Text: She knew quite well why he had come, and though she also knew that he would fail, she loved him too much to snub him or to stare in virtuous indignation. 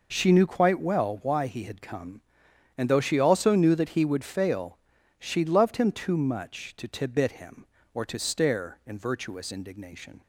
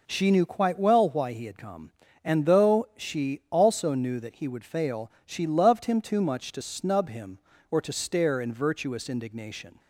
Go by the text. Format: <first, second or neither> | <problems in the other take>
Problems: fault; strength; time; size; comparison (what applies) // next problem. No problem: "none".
second | says "tibit" for "snub"; at 6.8 s